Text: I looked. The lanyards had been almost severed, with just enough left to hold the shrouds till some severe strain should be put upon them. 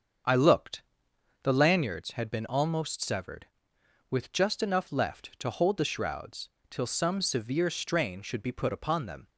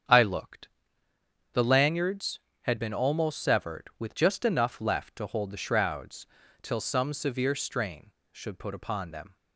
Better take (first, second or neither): first